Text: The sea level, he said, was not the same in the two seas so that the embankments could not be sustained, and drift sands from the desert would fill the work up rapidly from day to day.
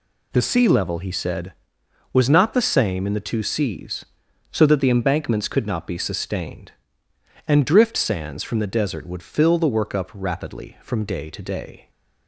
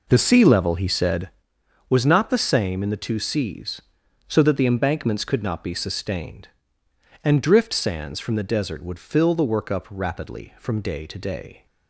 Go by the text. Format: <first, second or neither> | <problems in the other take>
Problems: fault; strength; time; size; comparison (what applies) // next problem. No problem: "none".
first | starts louder than the rest; noticeable; until 1.4 s; 4.5 dB